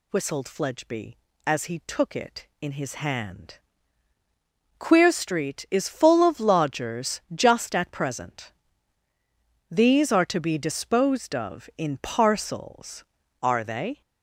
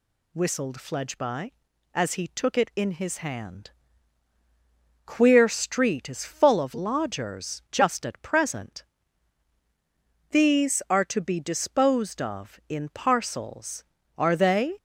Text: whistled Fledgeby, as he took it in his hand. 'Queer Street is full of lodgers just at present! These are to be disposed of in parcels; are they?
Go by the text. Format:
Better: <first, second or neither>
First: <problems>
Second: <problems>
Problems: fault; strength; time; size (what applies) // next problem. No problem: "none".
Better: neither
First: none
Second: none